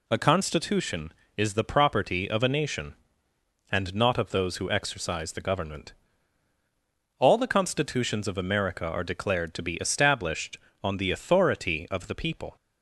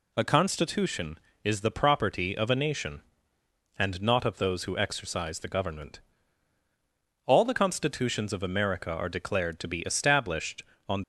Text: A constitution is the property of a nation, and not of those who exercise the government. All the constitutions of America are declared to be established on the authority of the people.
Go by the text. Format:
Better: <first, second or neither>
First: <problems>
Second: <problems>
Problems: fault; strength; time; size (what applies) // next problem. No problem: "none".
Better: first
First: none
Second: stops before "the authority of the people"; at 11.0 s